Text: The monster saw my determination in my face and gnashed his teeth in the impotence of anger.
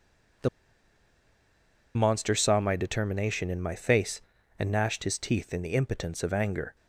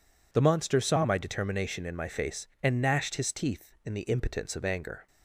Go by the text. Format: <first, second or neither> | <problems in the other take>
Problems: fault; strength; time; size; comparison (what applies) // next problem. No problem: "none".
second | pauses between "The" and "monster"; strong; at 0.4 s; 1.4 s long